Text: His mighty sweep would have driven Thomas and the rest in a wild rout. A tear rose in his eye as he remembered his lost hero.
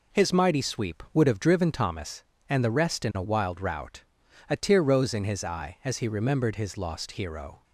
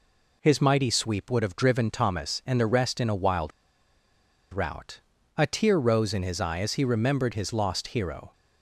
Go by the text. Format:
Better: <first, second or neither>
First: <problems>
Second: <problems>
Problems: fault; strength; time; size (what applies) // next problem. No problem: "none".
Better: first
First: none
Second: pauses between "wild" and "rout"; at 3.5 s; 1.0 s long